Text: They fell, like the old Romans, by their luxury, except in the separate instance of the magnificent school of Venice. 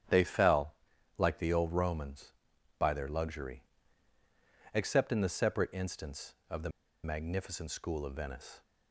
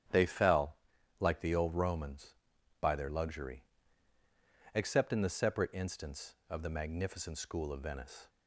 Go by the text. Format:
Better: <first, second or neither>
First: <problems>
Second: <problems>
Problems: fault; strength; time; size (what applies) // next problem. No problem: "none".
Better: second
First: starts louder than the rest; strong; until 1.5 s; 10 dB // pauses between "the" and "magnificent"; slight; at 6.6 s; 0.34 s long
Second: starts louder than the rest; strong; until 1.5 s; 9.5 dB